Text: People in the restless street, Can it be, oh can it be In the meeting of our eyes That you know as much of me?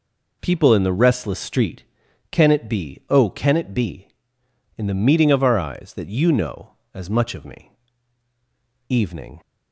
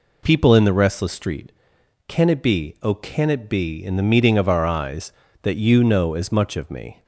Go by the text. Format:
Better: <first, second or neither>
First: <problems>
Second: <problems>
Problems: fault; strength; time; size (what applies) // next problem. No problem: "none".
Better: second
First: goes on to say "Evening"; from 8.8 s on; 0.52 s long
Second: none